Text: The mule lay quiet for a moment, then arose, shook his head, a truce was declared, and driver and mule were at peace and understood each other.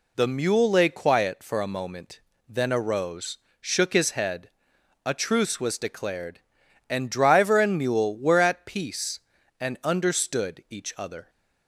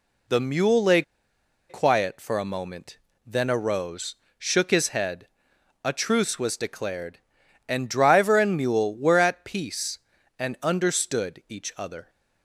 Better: first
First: none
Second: pauses between "lay" and "quiet"; noticeable; at 1.0 s; 0.66 s long

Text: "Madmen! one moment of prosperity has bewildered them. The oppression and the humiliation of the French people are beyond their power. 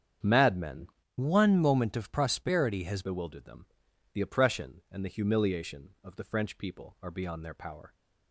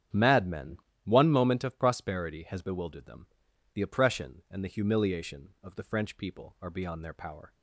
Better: second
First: starts louder than the rest; strong; until 1.5 s; 8 dB // changes voice from "one" to "has"; from 1.1 to 3.0 s; 1.9 s long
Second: starts louder than the rest; strong; until 1.3 s; 9 dB

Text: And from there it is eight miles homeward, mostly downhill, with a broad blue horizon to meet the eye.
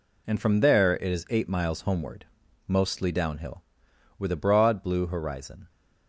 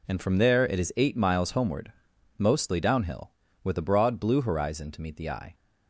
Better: second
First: stops before "to meet the eye"; at 5.6 s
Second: none

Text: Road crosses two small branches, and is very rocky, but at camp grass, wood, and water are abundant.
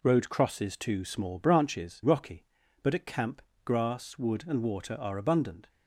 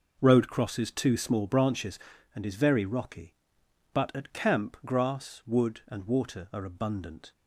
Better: second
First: skips "and is very"; at 2.0 s // pauses between "camp" and "grass"; slight; at 3.4 s; 0.24 s long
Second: none

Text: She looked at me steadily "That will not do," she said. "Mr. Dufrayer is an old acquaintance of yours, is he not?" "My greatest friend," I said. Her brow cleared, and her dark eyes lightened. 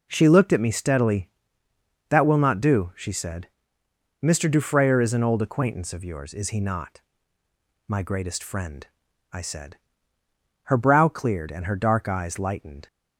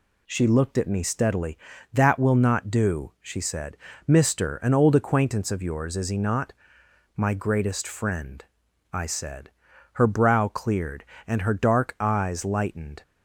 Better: first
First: none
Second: skips "Dufrayer is"; at 4.5 s

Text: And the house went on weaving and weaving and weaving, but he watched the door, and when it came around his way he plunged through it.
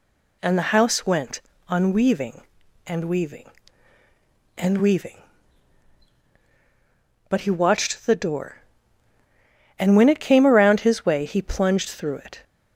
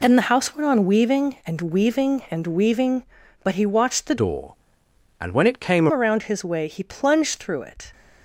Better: first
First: none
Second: changes voice from "door" to "came"; from 4.1 to 5.8 s; 1.7 s long

